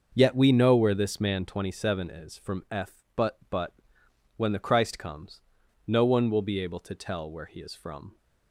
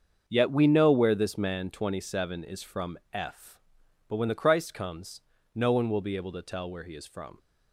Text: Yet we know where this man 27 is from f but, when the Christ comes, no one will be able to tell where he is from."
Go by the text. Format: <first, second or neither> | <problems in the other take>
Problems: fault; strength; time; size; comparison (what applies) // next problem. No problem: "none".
second | starts louder than the rest; until 1.1 s; 6 dB; also in the second // says "but" twice; at 3.4 s